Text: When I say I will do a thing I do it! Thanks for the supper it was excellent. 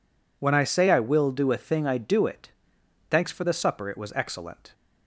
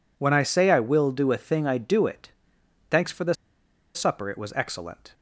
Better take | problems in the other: first | pauses between "the" and "supper"; noticeable; at 3.3 s; 0.60 s long

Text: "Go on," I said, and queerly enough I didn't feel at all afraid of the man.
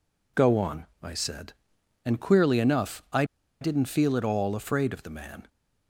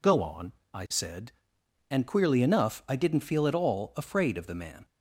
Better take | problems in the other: second | pauses between "I" and "didn't"; at 3.2 s; 0.37 s long

